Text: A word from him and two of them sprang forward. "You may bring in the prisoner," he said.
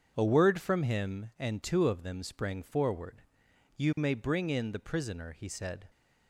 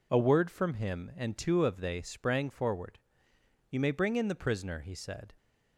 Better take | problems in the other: first | says "they" for "them"; at 1.7 s

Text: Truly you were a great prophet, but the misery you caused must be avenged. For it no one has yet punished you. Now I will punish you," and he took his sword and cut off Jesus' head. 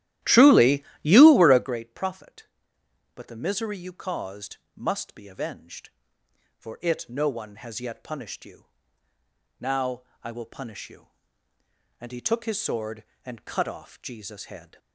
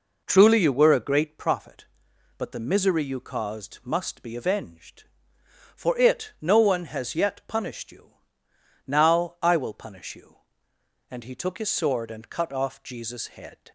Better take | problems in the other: second | starts louder than the rest; strong; until 1.8 s; 13.5 dB // pauses between "Truly" and "you"; slight; at 0.8 s; 0.18 s long // pauses between "caused" and "must"; slight; at 4.5 s; 0.20 s long // pauses between "Now" and "I"; slight; at 10.0 s; 0.20 s long

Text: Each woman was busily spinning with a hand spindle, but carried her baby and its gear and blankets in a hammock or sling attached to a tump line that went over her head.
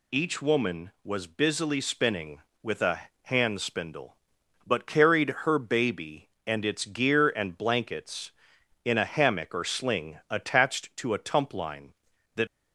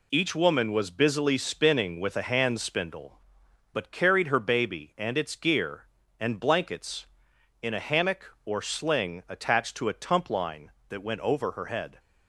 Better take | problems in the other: second | pauses between "a" and "hand"; slight; at 3.0 s; 0.22 s long // stops before "went over her head"; at 12.4 s

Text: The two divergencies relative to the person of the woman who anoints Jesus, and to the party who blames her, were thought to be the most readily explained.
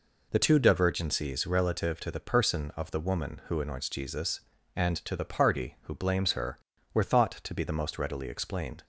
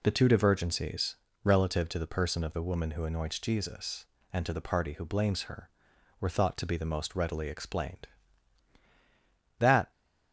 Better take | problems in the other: first | pauses between "divergencies" and "relative"; slight; at 1.1 s; 0.28 s long // goes on to say "That"; slight; from 9.5 s on; 0.32 s long

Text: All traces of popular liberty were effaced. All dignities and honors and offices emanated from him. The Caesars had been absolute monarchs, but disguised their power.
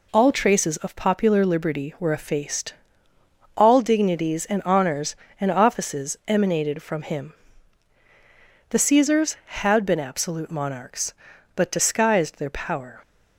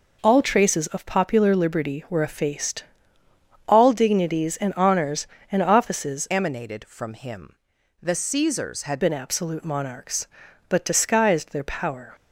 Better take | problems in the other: first | changes voice from "emanated" to "had"; from 6.2 to 9.0 s; 2.8 s long

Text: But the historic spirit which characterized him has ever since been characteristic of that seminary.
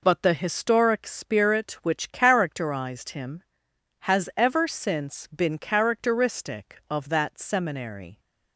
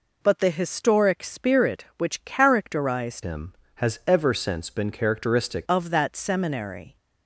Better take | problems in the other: first | changes voice from "him" to "characteristic"; from 3.2 to 5.6 s; 2.4 s long

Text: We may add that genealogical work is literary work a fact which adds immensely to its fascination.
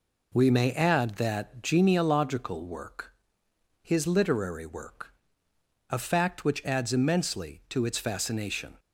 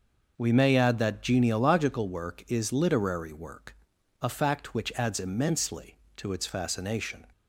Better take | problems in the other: second | says "his" for "is"; at 3.8 s // pauses between "work" and "a"; noticeable; at 5.1 s; 0.78 s long; noticeable in the second

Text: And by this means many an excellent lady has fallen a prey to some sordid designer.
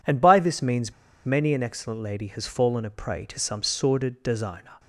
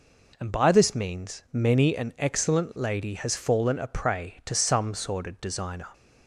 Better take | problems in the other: second | pauses between "means" and "many"; slight; at 0.9 s; 0.32 s long

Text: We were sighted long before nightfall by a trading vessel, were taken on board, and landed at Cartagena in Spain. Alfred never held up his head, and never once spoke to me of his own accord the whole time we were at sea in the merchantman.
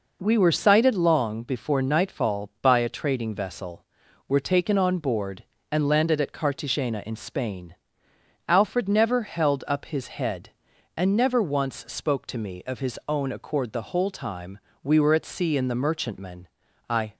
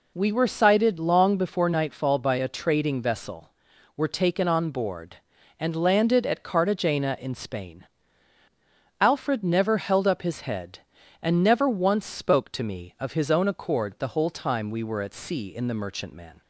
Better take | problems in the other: second | pauses between "time" and "we"; slight; at 14.5 s; 0.24 s long // goes on to say "I"; slight; from 16.8 s on; 0.28 s long

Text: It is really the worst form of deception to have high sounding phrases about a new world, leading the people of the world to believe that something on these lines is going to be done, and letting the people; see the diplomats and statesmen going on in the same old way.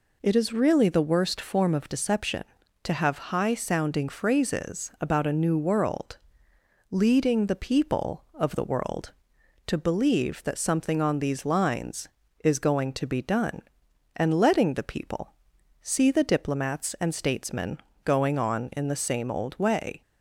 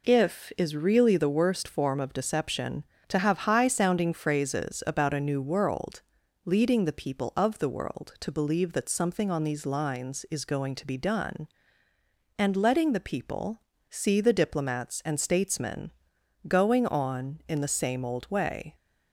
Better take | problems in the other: first | says "If" for "It"; at 0.0 s // pauses between "statesmen" and "going"; noticeable; at 15.9 s; 0.56 s long; slight in the first

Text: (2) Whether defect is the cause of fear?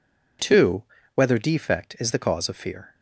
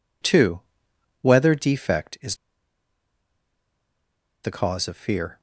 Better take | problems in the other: first | pauses between "is" and "the"; strong; at 2.3 s; 2.0 s long

